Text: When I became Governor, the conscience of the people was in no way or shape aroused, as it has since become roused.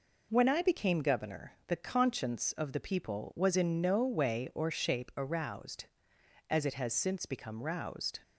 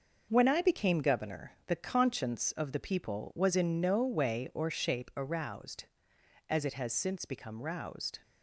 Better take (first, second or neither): first